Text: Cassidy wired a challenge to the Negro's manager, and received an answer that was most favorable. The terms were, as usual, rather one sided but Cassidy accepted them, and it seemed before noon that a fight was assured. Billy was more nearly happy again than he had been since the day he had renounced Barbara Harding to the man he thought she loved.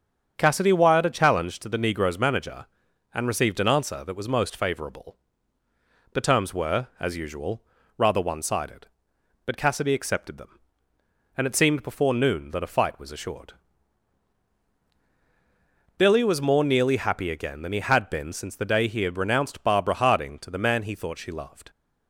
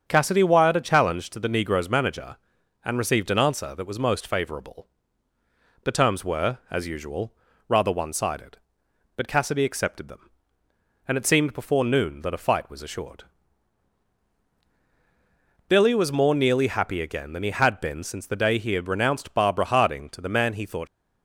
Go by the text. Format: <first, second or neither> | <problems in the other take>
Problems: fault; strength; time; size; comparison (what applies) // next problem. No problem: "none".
first | starts louder than the rest; until 1.0 s; 7 dB; also in the first // stops before "she loved"; at 20.8 s